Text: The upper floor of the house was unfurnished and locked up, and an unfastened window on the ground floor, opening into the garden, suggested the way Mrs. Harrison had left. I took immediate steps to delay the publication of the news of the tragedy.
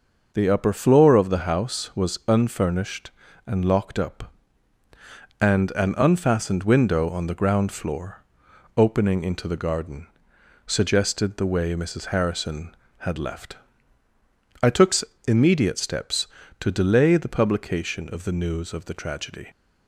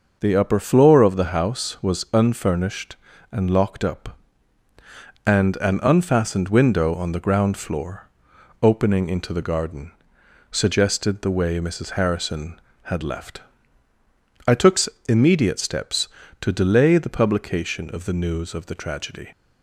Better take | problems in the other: neither | pauses between "took" and "immediate"; slight; the same in both

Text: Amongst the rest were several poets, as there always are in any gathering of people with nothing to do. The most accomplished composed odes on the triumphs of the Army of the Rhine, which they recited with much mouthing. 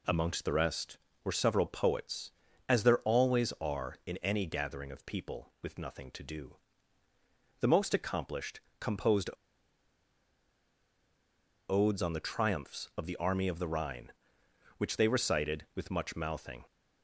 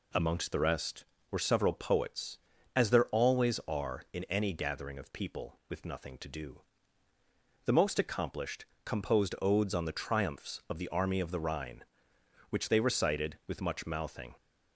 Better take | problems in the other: second | pauses between "accomplished" and "composed"; slight; at 8.5 s; 0.20 s long; slight in the second // pauses between "composed" and "odes"; strong; at 9.2 s; 2.3 s long

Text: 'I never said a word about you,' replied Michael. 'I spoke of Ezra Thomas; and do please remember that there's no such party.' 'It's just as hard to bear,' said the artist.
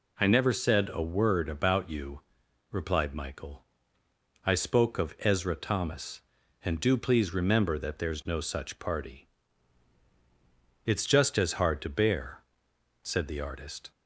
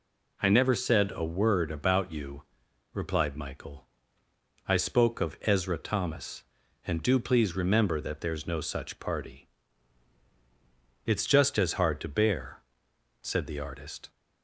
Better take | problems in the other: neither | none

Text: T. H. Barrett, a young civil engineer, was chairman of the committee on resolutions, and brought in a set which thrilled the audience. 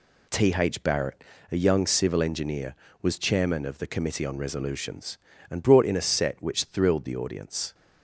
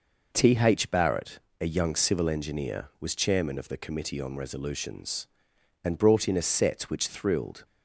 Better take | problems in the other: first | stops before "the audience"; at 7.6 s

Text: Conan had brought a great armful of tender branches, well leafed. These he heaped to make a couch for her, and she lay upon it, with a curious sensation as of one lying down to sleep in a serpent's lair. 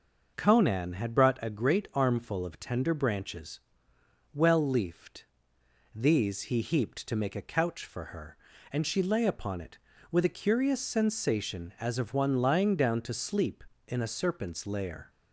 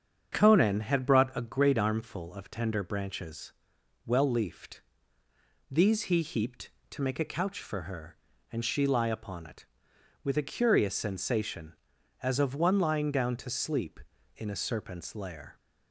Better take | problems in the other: first | starts louder than the rest; strong; until 1.4 s; 7.5 dB // says "lie" for "lay"; at 8.8 s

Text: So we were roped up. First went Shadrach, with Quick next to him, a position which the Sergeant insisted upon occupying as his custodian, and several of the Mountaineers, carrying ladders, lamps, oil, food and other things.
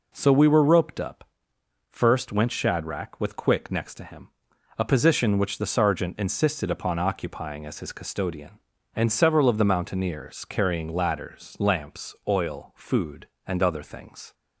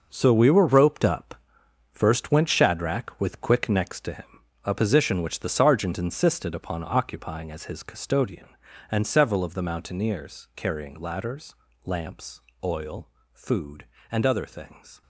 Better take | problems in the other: first | gets quieter; strong; throughout; 11.5 dB

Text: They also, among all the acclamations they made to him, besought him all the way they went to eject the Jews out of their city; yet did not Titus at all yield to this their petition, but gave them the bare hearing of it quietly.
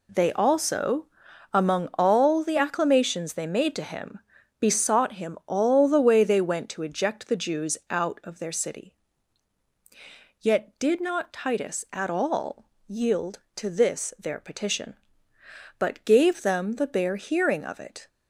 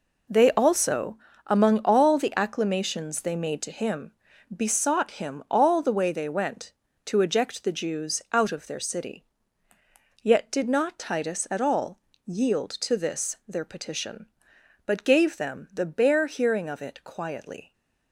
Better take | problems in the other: second | pauses between "all" and "yield"; slight; at 12.6 s; 0.22 s long; slight in the second // stops before "quietly"; at 18.0 s

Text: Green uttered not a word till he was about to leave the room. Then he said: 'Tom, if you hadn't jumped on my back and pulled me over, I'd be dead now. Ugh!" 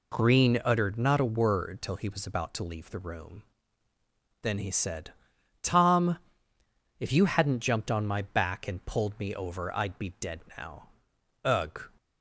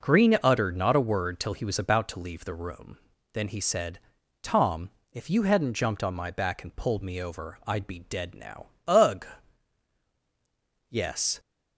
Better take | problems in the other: first | goes on to say "Yes"; from 10.8 s on; 0.50 s long

